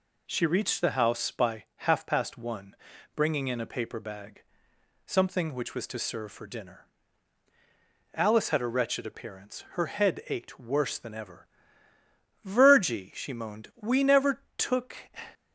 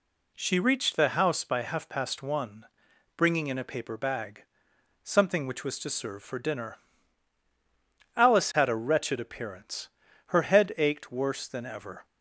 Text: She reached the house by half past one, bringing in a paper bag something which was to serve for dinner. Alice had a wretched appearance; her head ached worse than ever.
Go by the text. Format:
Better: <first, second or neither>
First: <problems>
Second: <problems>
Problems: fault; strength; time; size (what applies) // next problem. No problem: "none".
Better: second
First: pauses between "bag" and "something"; noticeable; at 4.4 s; 0.66 s long // goes on to say "Virgie she moaned we never took"; strong; from 12.4 s on; 2.5 s long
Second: pauses between "bag" and "something"; noticeable; at 4.4 s; 0.62 s long